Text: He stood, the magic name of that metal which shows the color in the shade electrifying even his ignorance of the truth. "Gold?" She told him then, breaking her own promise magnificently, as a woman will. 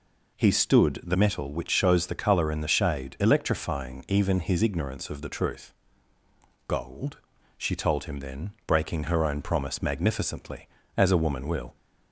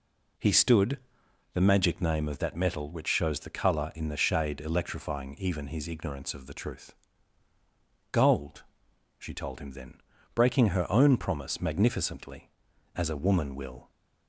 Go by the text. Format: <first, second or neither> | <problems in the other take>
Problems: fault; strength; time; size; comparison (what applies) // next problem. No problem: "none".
second | skips "magic name of that"; at 1.1 s